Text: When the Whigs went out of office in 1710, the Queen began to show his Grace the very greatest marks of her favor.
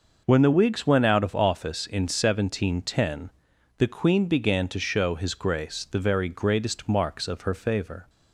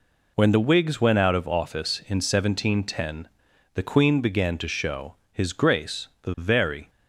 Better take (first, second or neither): first